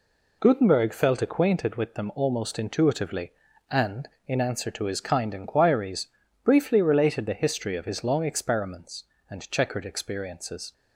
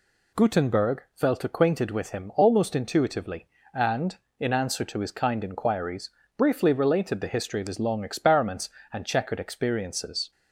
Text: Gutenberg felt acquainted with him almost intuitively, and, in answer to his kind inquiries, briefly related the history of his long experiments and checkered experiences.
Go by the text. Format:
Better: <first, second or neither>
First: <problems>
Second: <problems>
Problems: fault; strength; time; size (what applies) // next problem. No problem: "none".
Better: second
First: says "them" for "him"; at 1.9 s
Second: none